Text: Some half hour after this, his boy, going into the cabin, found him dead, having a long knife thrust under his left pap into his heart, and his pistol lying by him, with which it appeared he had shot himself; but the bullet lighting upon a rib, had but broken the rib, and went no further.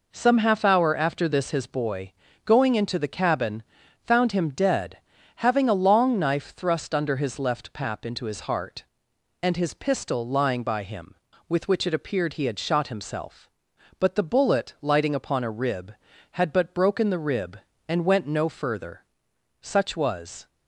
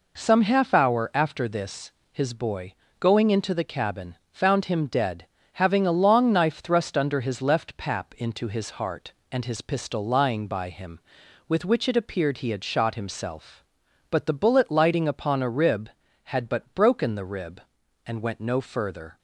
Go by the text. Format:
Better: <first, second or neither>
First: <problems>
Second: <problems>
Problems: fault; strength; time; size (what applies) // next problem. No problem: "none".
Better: second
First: goes on to say "Such was"; noticeable; from 19.6 s on; 0.86 s long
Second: none